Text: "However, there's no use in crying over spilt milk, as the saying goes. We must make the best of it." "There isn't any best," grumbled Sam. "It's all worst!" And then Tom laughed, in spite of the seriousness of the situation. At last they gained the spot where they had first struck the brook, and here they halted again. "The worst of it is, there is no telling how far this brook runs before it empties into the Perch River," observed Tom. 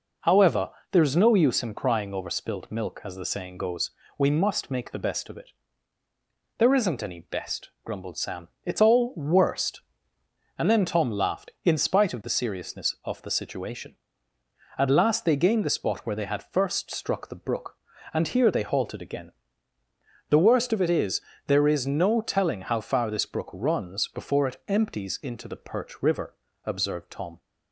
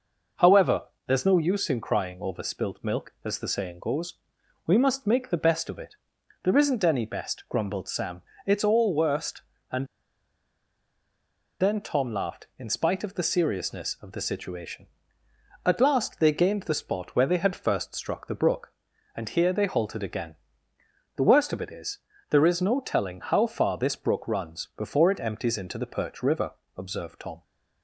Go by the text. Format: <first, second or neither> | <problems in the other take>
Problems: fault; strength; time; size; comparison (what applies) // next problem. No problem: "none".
first | pauses between "And" and "then"; strong; at 9.8 s; 1.7 s long